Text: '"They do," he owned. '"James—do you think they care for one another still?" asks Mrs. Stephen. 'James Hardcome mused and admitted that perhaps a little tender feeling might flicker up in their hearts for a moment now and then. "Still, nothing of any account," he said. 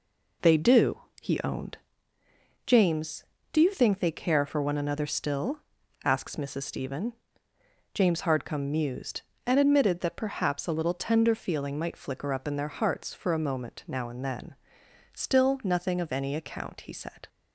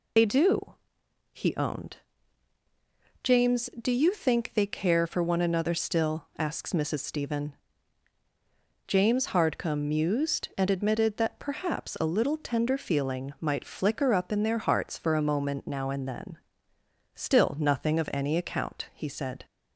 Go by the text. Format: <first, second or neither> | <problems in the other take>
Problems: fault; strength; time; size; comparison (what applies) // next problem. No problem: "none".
first | loses the start of "They"; at 0.1 s; 55 ms